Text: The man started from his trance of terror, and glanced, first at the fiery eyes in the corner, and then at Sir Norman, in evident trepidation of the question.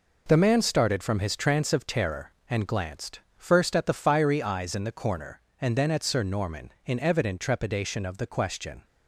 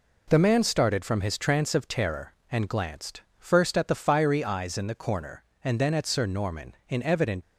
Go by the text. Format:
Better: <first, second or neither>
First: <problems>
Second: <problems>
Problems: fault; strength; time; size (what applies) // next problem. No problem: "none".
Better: first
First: none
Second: stops before "trepidation of the question"; at 7.4 s